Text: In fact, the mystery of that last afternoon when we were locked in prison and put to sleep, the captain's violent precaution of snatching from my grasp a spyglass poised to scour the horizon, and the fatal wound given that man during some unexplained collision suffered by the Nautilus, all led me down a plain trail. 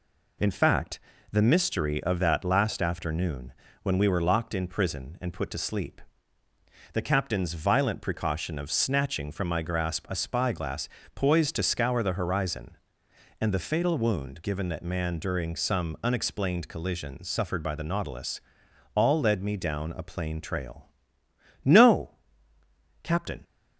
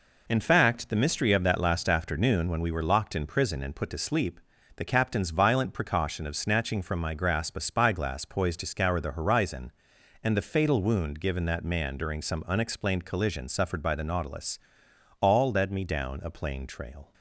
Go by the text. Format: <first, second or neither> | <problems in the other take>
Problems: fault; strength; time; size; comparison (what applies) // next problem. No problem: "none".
second | pauses between "afternoon" and "when"; slight; at 3.5 s; 0.32 s long // pauses between "spyglass" and "poised"; slight; at 10.8 s; 0.26 s long // goes on to say "No Captain"; strong; from 21.6 s on; 1.8 s long